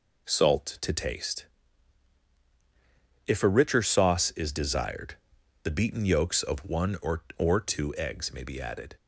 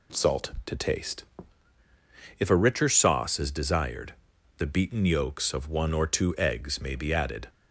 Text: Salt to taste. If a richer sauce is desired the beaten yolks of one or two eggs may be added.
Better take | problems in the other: second | pauses between "desired" and "the"; noticeable; at 5.1 s; 0.48 s long; also in the second // says "or" twice; at 7.3 s

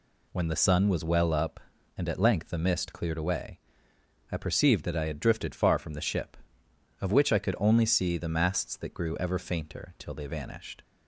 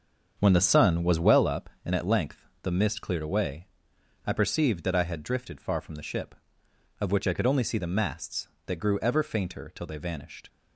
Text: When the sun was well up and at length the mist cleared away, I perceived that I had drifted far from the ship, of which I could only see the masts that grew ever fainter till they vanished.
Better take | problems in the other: first | starts louder than the rest; until 1.5 s; 7 dB // pauses between "length" and "the"; slight; at 2.4 s; 0.16 s long

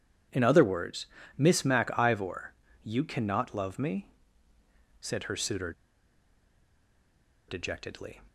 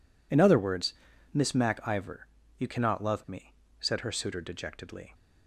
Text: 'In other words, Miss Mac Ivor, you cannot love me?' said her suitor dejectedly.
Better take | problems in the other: second | pauses between "suitor" and "dejectedly"; strong; at 5.7 s; 1.7 s long

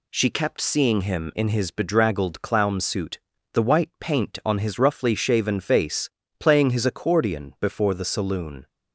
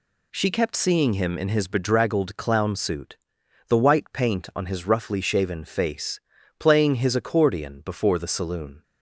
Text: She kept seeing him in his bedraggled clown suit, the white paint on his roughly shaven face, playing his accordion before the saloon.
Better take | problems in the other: neither | none

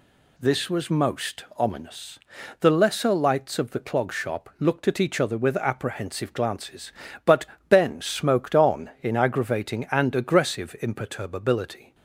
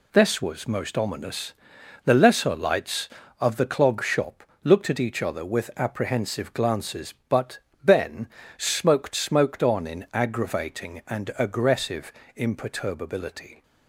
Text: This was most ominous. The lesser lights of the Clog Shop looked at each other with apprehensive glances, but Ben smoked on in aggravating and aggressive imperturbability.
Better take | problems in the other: first | pauses between "Shop" and "looked"; slight; at 4.4 s; 0.22 s long // pauses between "but" and "Ben"; slight; at 7.5 s; 0.26 s long; slight in the first // pauses between "Ben" and "smoked"; slight; at 8.2 s; 0.32 s long // says "smoked" twice; at 9.1 s // pauses between "aggressive" and "imperturbability"; slight; at 12.1 s; 0.24 s long

